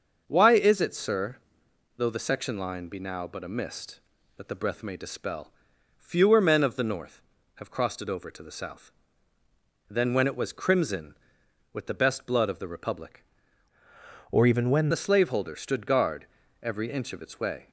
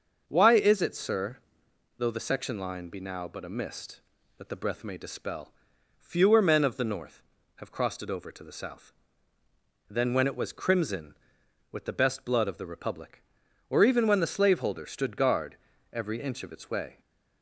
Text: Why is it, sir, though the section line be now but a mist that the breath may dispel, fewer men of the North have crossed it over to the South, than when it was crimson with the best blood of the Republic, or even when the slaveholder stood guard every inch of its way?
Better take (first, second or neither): second